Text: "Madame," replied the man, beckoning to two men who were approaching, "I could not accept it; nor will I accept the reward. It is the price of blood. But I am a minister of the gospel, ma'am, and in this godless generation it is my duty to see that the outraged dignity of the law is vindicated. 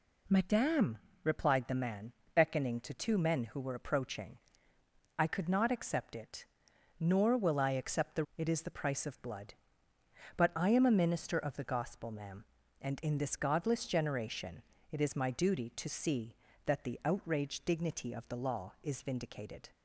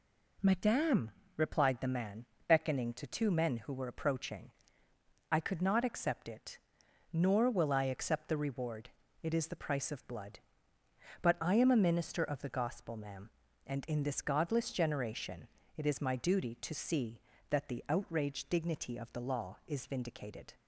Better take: second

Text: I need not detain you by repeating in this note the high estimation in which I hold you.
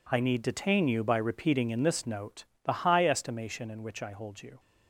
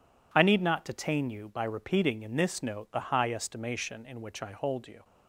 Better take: second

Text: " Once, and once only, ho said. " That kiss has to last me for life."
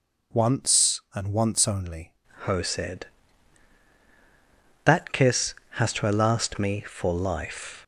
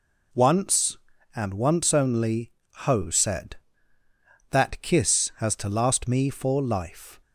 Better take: second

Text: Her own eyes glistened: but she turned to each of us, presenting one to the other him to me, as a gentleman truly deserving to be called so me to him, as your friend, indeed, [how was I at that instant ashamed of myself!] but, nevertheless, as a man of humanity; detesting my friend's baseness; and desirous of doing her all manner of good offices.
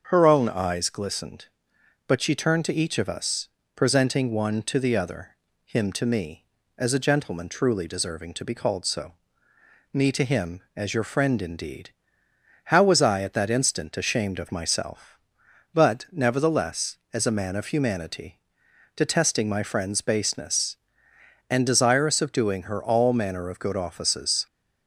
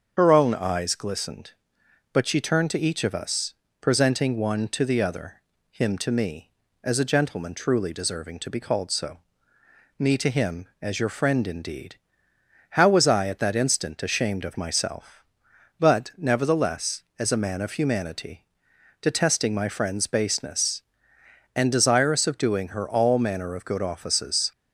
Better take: first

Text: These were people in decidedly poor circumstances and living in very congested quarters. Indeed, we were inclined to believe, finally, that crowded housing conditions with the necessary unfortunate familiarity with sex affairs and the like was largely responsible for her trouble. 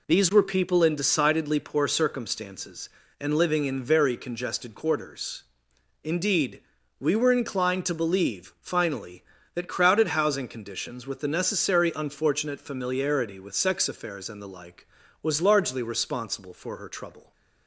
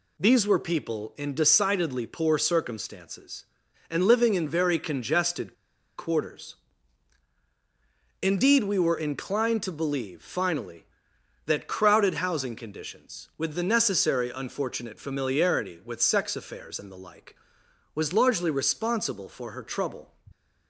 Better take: first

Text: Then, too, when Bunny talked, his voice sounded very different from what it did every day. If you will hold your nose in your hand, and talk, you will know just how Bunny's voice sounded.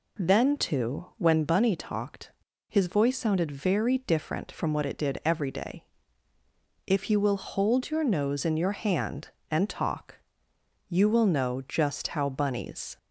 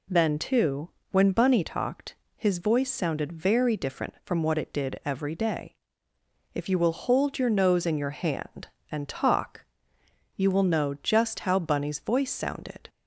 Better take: second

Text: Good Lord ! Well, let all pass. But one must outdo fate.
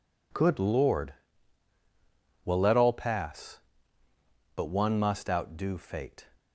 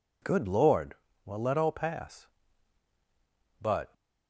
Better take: first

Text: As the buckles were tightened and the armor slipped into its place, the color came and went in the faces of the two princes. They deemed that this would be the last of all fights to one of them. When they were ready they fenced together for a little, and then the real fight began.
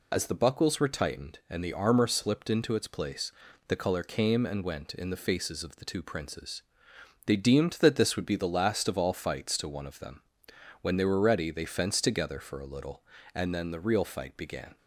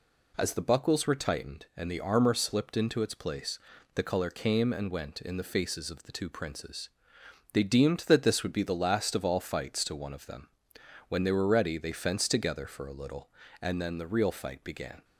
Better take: second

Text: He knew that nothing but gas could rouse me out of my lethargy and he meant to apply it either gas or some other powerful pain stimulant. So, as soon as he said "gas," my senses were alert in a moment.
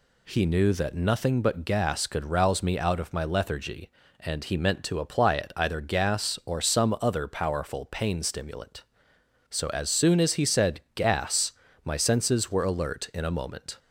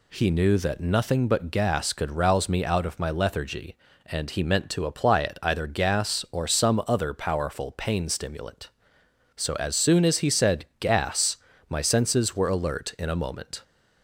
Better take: neither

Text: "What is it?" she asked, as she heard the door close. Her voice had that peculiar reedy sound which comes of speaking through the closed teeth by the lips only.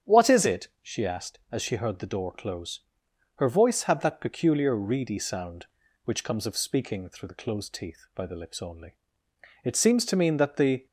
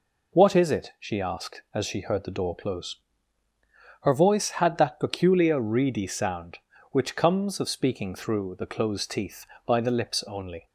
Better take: second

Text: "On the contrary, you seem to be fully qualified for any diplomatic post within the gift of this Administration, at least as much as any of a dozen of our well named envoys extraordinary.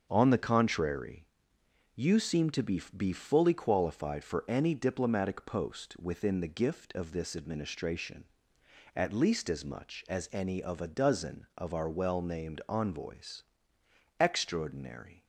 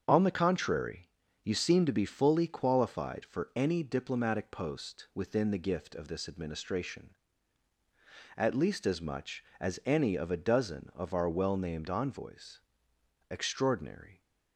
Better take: second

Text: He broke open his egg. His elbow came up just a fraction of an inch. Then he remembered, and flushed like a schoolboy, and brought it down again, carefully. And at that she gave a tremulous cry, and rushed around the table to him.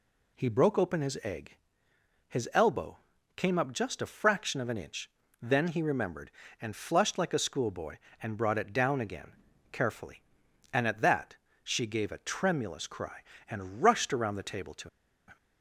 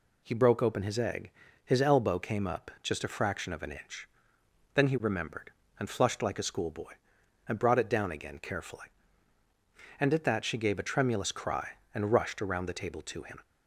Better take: second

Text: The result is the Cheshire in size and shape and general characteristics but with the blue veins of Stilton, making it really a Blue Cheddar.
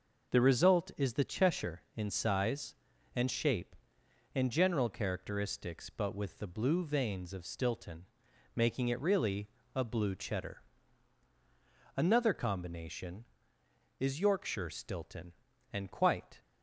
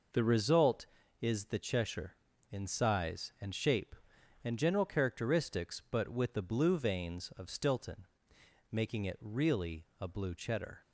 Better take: second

